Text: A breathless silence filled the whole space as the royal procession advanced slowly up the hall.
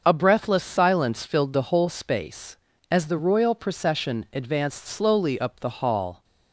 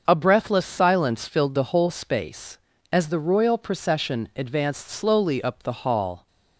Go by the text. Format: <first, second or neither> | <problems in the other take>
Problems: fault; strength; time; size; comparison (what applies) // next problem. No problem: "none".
neither | starts louder than the rest; the same in both